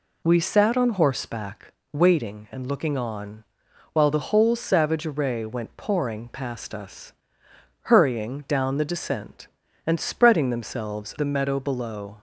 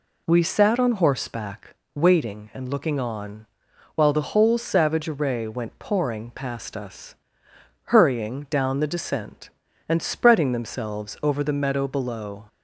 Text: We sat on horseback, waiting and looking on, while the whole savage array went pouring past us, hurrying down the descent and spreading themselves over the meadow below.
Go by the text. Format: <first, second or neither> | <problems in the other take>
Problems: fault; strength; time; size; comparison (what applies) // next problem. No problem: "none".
second | skips "over"; at 11.1 s